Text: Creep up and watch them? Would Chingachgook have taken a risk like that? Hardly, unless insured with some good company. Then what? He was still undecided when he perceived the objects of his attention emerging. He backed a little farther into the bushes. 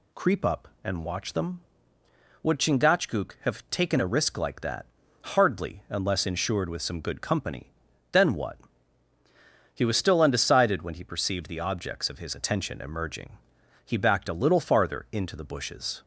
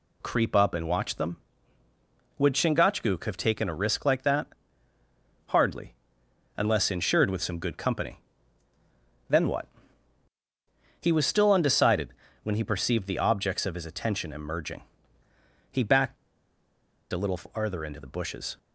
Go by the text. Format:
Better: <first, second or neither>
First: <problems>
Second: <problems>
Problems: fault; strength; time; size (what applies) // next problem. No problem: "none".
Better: first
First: none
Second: pauses between "undecided" and "when"; slight; at 12.0 s; 0.34 s long // pauses between "backed" and "a"; noticeable; at 16.1 s; 0.97 s long